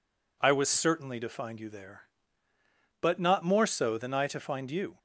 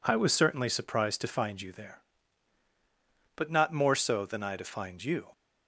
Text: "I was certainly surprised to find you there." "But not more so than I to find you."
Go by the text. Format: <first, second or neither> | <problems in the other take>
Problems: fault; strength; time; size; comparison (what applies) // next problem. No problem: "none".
second | skips "surprised"; at 1.1 s